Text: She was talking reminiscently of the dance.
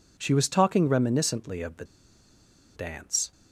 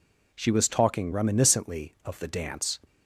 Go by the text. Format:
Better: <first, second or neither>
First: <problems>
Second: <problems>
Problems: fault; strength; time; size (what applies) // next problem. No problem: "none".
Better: second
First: pauses between "the" and "dance"; noticeable; at 1.8 s; 0.91 s long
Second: none